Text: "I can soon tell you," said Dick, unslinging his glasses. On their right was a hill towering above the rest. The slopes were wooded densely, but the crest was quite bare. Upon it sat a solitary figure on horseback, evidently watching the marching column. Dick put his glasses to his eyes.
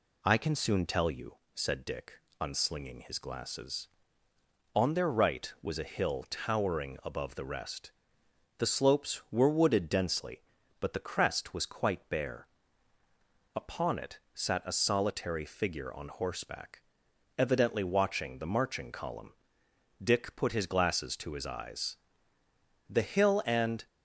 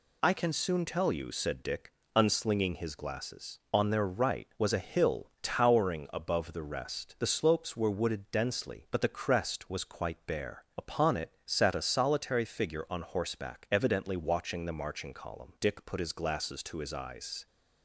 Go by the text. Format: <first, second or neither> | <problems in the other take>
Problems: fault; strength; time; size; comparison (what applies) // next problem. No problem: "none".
second | goes on to say "The hill and"; noticeable; from 22.8 s on; 0.98 s long